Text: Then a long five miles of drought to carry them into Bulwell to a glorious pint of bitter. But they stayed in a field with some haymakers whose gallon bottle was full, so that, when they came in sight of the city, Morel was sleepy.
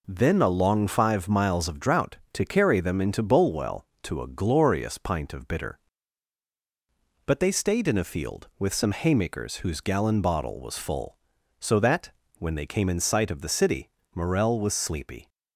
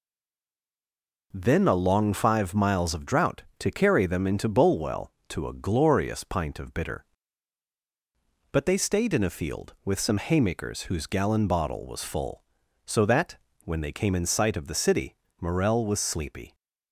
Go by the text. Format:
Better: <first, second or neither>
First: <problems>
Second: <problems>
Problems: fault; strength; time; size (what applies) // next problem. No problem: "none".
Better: first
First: none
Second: stays silent before the first word; noticeable; until 1.3 s; 1.3 s long